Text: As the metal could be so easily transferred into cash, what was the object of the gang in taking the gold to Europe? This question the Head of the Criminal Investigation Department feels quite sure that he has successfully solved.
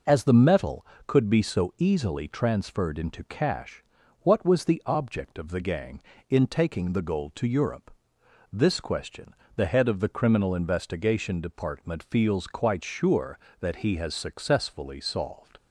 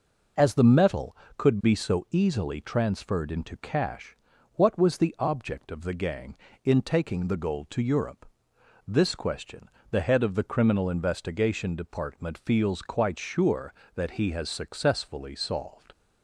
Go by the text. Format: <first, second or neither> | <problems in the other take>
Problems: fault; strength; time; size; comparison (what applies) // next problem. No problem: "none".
neither | pauses between "question" and "the"; slight; the same in both